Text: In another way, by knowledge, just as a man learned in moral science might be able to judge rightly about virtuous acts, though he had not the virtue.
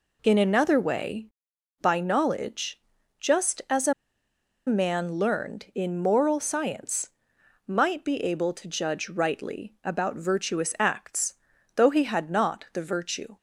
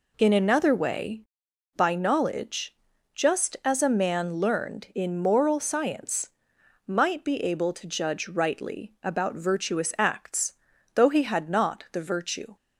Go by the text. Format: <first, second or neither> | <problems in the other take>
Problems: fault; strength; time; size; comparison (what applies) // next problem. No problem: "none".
second | pauses between "a" and "man"; noticeable; at 3.9 s; 0.73 s long // pauses between "science" and "might"; noticeable; at 7.0 s; 0.58 s long; noticeable in the second